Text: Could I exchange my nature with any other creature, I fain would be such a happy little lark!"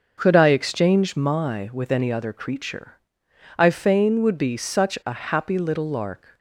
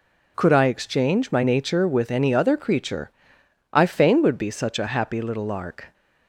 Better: second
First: skips "nature"; at 1.6 s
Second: none

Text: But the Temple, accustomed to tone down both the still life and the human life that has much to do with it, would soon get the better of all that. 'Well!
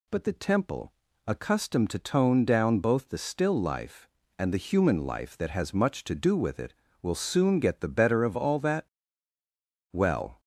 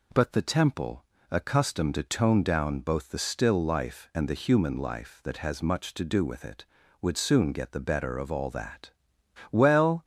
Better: second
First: says "will" for "would"; at 7.0 s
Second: none

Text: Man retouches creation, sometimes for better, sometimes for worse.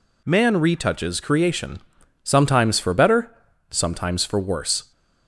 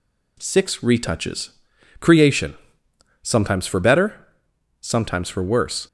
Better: first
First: none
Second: says "Six" for "Man"; at 0.3 s // pauses between "retouches" and "creation"; noticeable; at 1.5 s; 0.48 s long

